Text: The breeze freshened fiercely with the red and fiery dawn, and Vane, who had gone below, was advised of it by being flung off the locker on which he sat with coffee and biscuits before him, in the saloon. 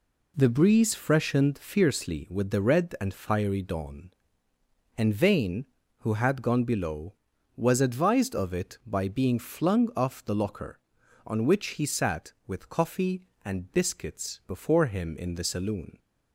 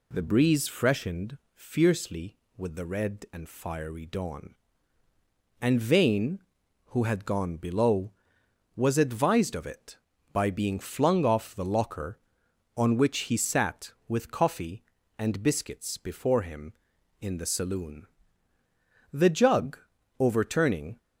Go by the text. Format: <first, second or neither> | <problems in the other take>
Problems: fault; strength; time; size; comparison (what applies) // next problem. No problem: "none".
first | pauses between "freshened" and "fiercely"; slight; at 1.3 s; 0.16 s long // goes on to say "The jug overturning"; strong; from 19.1 s on; 1.8 s long